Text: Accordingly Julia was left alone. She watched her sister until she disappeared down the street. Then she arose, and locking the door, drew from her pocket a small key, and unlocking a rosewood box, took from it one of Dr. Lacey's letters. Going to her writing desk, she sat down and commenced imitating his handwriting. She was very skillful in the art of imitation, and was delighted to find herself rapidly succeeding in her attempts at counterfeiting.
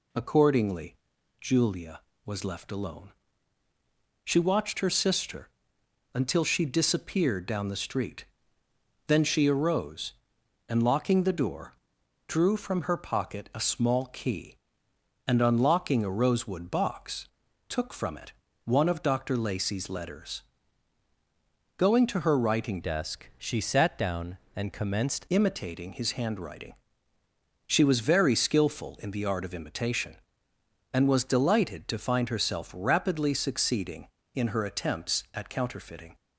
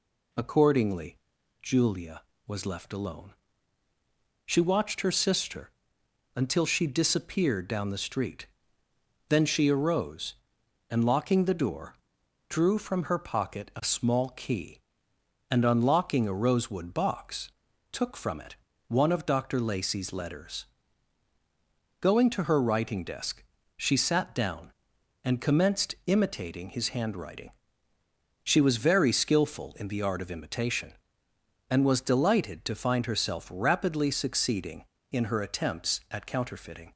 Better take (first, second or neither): second